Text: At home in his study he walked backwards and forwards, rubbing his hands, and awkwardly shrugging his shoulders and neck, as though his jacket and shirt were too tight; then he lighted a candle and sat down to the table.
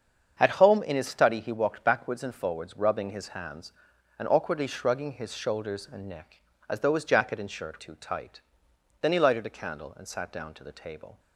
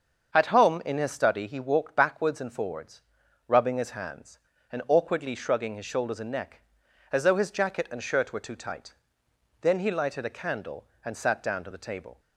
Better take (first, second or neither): second